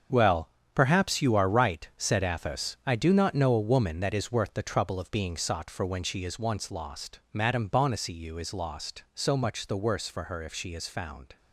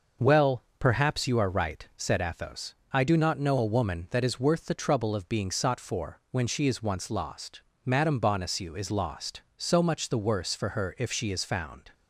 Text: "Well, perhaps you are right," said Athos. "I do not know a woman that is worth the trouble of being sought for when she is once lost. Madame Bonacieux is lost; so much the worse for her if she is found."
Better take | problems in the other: second | gets quieter; strong; throughout; 10.5 dB

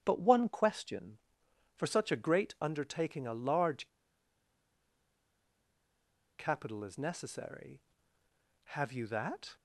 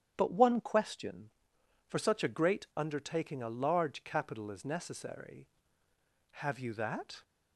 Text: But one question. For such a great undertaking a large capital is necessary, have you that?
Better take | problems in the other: second | starts louder than the rest; strong; until 1.0 s; 9.5 dB; strong in the second // pauses between "large" and "capital"; strong; at 3.8 s; 2.4 s long

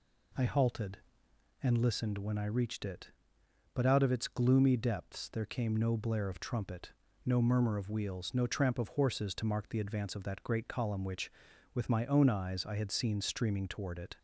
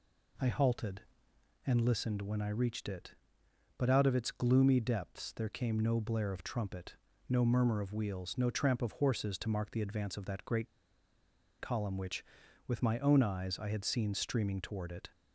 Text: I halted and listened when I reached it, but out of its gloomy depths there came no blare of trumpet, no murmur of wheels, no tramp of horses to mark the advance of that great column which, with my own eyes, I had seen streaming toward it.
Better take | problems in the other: first | pauses between "great" and "column"; noticeable; at 10.6 s; 0.91 s long

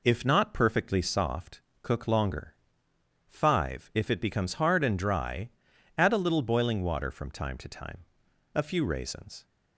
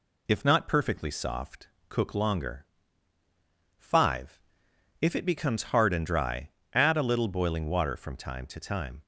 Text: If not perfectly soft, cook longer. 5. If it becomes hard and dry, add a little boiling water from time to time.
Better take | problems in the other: second | goes on to say "A few raisins"; noticeable; from 8.5 s on; 0.92 s long

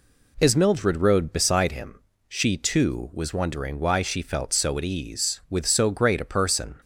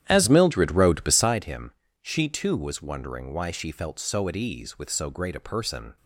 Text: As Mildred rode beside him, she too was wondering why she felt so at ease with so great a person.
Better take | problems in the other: first | starts louder than the rest; strong; until 1.5 s; 11 dB

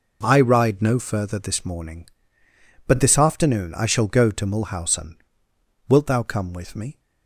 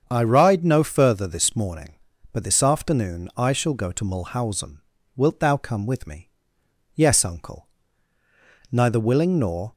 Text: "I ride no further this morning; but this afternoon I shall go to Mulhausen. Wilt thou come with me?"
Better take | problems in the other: first | starts louder than the rest; strong; until 1.1 s; 7 dB // goes on to say "Yes uncle Neither willing nor"; strong; from 6.9 s on; 2.7 s long

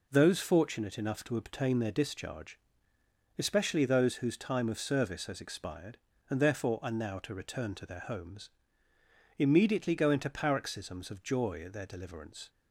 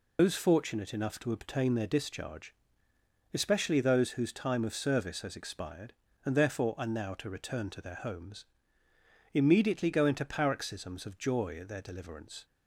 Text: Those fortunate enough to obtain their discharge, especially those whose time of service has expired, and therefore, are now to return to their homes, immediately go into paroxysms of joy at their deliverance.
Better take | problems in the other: first | loses the start of "Those"; at 0.1 s; 145 ms

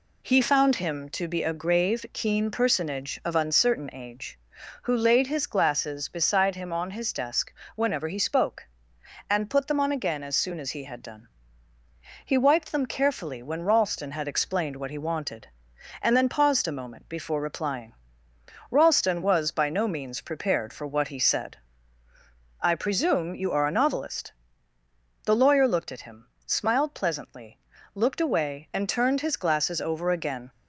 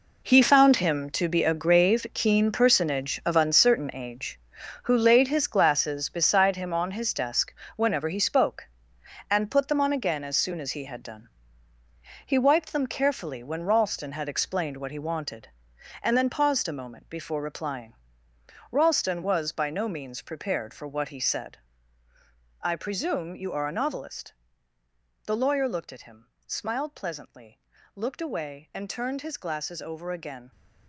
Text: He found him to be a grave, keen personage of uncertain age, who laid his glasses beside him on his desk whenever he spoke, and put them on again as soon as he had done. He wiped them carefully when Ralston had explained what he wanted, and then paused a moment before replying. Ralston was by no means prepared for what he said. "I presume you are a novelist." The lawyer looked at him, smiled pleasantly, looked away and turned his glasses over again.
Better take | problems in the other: first | gets quieter; strong; throughout; 12 dB // pauses between "desk" and "whenever"; slight; at 7.5 s; 0.24 s long; slight in the first

